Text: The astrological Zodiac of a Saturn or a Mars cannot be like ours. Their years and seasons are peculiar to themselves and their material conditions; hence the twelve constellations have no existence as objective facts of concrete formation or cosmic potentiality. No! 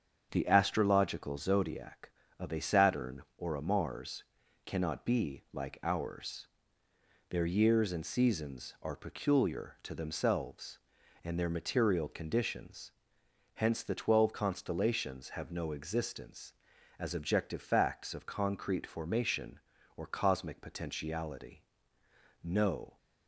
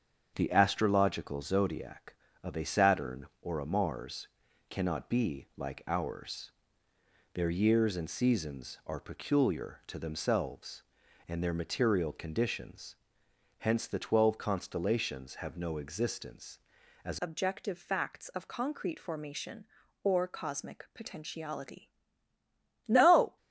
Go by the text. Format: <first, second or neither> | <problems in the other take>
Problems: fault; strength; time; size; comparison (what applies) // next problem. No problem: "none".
first | starts louder than the rest; strong; until 1.3 s; 7.5 dB; strong in the first // pauses between "Mars" and "cannot"; at 4.2 s; 0.42 s long; also in the first // changes voice at "objective"; from 17.2 s on; 6.1 s long